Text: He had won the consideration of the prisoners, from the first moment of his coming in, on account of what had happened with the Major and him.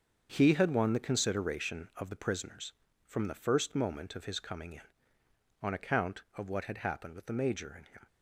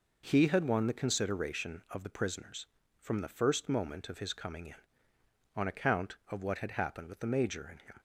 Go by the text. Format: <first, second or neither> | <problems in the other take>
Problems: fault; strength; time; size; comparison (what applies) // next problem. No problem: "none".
second | gets quieter; strong; throughout; 10 dB